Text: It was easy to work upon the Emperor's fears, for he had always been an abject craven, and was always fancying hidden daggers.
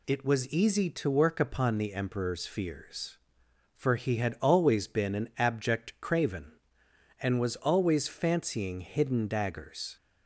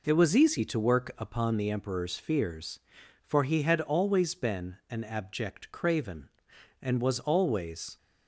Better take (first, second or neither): first